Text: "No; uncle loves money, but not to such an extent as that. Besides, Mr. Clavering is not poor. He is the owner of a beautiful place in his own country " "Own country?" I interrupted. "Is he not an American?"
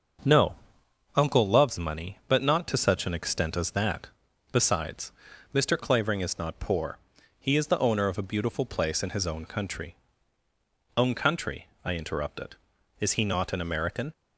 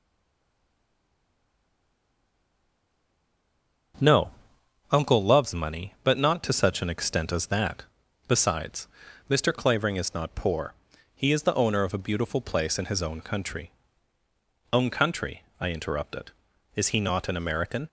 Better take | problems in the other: first | stays silent before the first word; strong; until 3.9 s; 3.9 s long // starts louder than the rest; until 5.6 s; 7 dB; also in the first

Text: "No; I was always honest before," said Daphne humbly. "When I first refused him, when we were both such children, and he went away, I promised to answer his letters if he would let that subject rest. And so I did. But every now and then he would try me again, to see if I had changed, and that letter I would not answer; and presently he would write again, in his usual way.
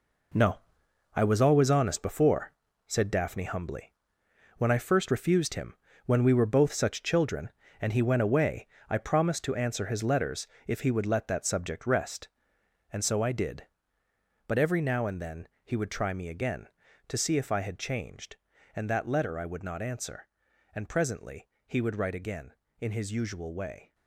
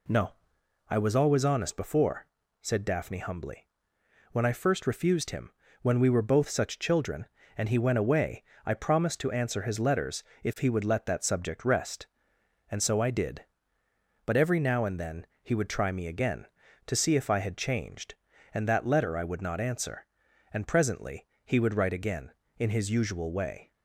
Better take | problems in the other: second | gets quieter; strong; throughout; 10 dB // pauses between "letters" and "if"; slight; at 10.4 s; 0.22 s long; slight in the second // pauses between "then" and "he"; slight; at 15.4 s; 0.16 s long; slight in the second // pauses between "presently" and "he"; slight; at 21.4 s; 0.18 s long; slight in the second

